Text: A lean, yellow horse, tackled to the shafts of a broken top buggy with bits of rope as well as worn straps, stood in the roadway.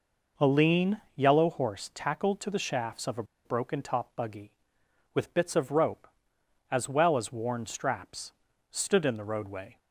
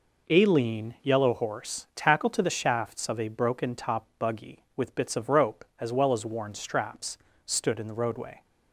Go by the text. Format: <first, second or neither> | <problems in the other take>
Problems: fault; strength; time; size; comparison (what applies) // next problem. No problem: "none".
second | pauses between "a" and "broken"; slight; at 3.2 s; 0.21 s long